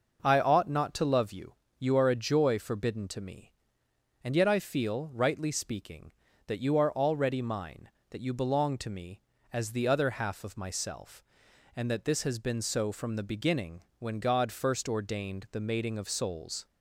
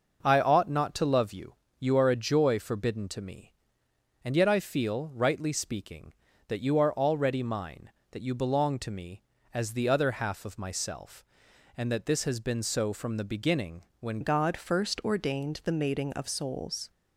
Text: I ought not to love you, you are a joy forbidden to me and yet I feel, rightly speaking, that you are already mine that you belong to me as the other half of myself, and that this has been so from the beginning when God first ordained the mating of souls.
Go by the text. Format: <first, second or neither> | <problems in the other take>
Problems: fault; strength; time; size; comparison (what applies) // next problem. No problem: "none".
first | pauses between "beginning" and "when"; slight; at 13.8 s; 0.18 s long; slight in the first // changes voice at "God"; from 14.2 s on; 2.6 s long